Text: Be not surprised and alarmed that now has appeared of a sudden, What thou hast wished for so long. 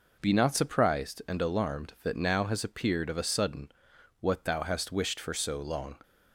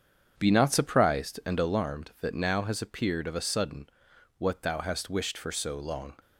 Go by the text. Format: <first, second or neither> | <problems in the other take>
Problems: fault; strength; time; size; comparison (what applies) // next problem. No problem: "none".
first | starts louder than the rest; strong; until 1.9 s; 7.5 dB